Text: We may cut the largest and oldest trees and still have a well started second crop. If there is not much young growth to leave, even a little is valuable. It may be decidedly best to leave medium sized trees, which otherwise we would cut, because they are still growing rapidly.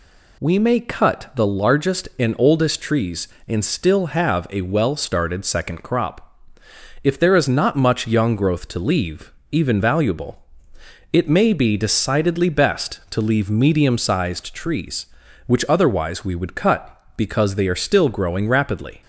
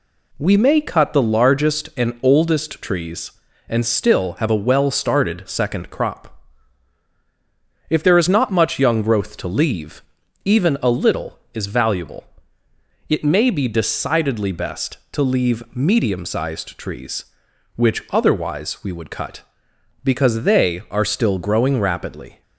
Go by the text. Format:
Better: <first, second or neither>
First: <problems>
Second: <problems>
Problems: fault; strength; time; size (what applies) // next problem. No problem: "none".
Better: second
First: skips "a little is"; at 9.8 s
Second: none